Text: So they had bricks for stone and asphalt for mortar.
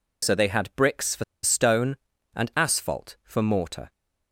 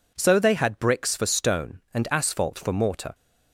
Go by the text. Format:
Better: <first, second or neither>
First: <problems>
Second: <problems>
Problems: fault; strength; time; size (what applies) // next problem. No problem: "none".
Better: second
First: pauses between "for" and "stone"; slight; at 1.2 s; 0.20 s long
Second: none